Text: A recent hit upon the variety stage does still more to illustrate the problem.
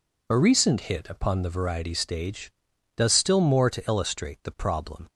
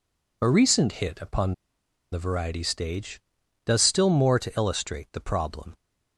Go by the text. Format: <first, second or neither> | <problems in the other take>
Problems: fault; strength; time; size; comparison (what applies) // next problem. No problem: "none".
first | pauses between "upon" and "the"; noticeable; at 1.5 s; 0.57 s long